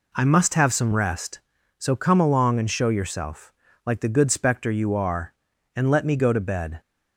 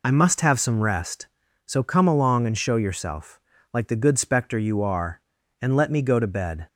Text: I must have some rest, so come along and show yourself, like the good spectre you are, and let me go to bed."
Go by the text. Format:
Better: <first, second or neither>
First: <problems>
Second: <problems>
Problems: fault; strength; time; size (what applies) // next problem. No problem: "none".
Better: first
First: none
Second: loses the start of "I"; at 0.0 s; 40 ms